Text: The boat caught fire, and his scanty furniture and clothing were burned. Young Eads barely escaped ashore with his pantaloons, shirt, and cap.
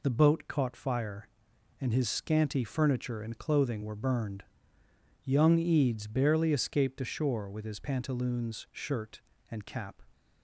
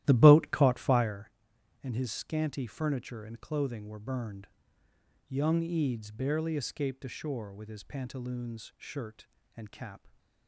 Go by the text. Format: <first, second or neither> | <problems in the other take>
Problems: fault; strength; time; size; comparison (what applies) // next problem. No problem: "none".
first | starts louder than the rest; strong; until 1.2 s; 14 dB